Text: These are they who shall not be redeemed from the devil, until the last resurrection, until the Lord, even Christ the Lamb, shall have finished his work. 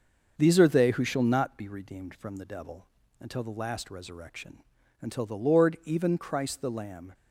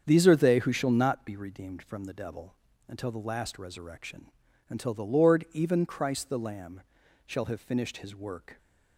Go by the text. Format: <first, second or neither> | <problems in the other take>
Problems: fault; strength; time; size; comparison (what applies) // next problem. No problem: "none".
second | starts louder than the rest; until 1.3 s; 6.5 dB; strong in the second // stops before "shall have finished his work"; at 7.1 s